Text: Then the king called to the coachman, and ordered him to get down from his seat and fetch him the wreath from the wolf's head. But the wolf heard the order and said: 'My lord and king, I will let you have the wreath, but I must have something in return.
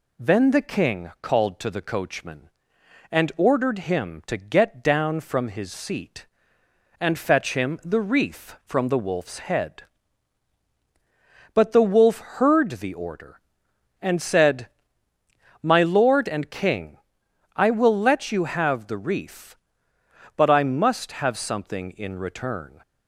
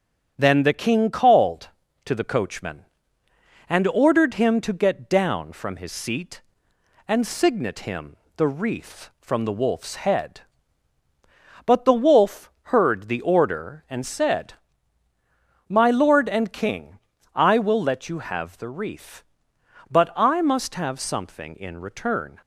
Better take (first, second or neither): first